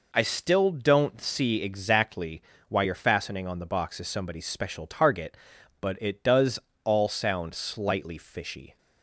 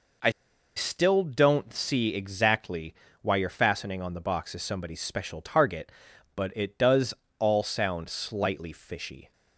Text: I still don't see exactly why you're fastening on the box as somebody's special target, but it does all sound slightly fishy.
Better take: first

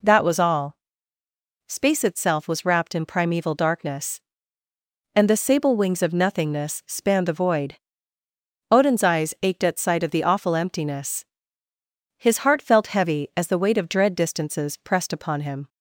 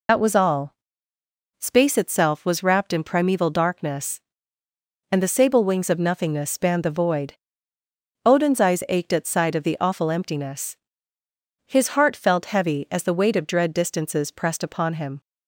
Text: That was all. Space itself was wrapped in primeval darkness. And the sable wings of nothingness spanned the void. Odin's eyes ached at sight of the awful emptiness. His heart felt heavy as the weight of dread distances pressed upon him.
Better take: first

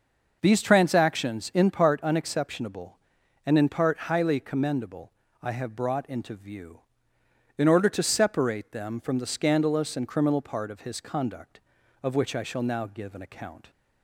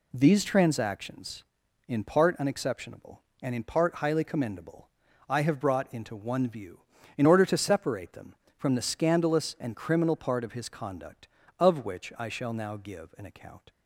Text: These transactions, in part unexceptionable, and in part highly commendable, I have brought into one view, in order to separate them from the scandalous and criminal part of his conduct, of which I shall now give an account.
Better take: second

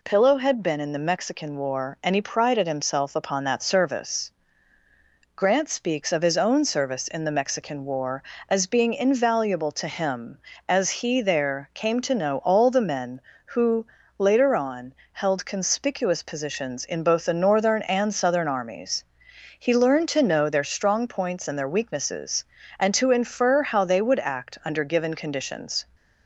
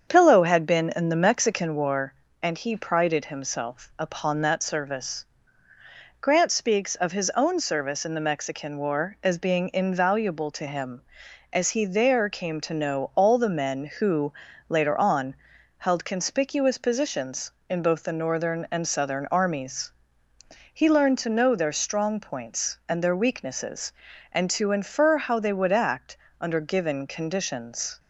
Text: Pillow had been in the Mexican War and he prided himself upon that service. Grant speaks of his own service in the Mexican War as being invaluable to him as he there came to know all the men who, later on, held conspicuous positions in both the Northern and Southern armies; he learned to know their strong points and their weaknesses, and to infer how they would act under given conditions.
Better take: first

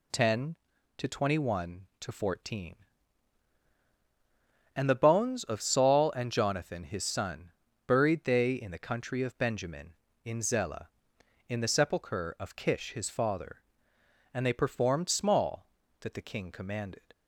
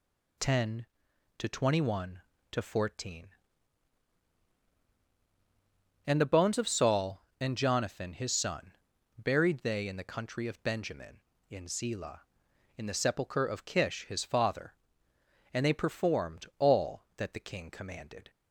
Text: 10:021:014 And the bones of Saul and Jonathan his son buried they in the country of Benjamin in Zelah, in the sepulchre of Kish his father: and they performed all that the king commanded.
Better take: second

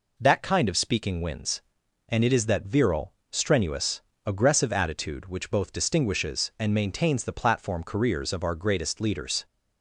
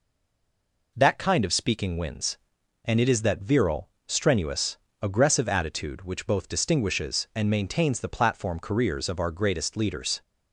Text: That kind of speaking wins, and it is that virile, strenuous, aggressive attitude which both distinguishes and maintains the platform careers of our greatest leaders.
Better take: first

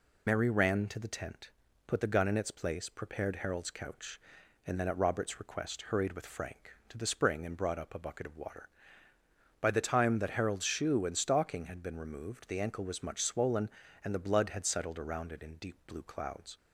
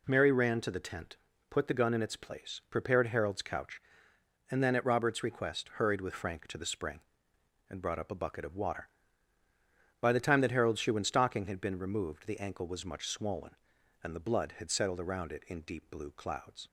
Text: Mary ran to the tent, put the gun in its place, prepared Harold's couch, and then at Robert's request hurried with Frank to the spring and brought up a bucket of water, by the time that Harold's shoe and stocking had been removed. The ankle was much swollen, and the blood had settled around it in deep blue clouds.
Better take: second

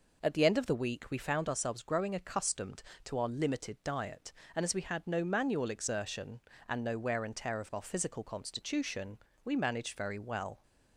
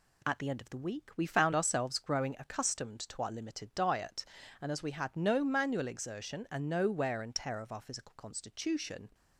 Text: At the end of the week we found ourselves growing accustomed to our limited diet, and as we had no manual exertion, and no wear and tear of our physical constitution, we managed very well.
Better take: first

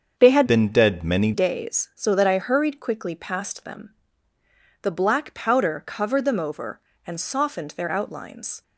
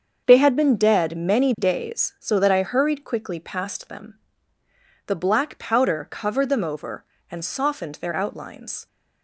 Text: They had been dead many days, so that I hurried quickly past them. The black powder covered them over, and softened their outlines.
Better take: second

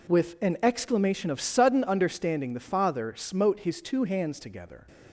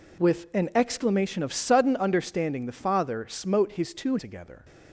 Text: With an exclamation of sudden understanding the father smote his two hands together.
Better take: first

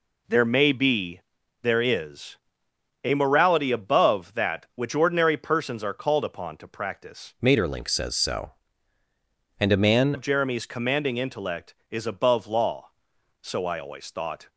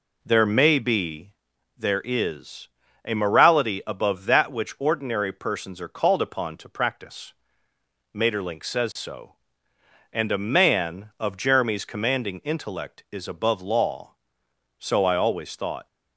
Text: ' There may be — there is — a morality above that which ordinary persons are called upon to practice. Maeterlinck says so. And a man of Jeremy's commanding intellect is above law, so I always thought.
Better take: second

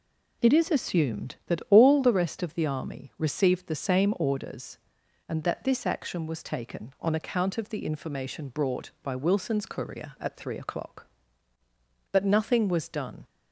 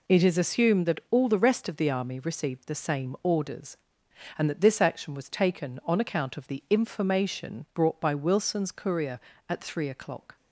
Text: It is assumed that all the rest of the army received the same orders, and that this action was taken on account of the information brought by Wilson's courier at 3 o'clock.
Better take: second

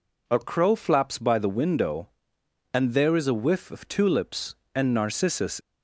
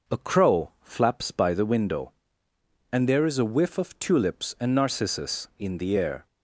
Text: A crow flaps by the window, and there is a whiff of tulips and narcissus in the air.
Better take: second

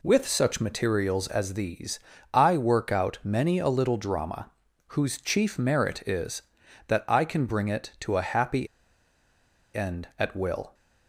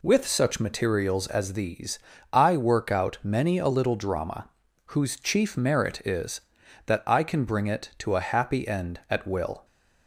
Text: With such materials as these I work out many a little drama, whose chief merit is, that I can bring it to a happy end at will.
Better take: second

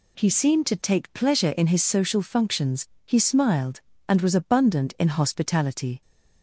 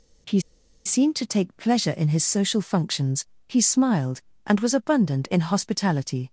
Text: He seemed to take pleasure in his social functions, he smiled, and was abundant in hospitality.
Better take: first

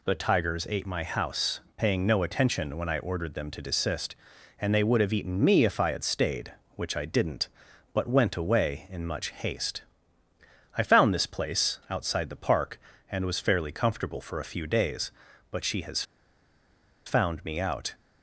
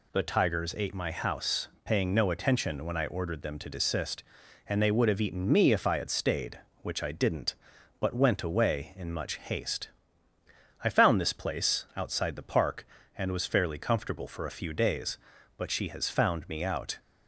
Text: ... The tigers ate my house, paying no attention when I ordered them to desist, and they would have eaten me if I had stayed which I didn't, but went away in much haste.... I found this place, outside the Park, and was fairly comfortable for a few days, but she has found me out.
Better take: second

